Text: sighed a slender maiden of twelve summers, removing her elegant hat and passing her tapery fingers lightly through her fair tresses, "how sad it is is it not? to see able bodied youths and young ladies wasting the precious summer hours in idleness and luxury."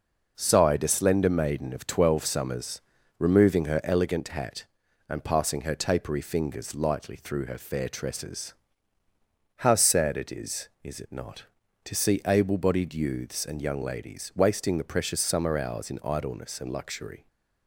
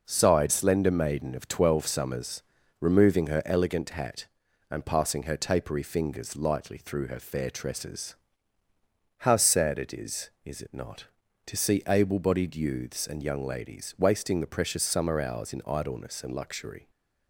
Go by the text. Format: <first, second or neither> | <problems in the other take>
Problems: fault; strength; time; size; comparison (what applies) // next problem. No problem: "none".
first | skips "a"; at 0.5 s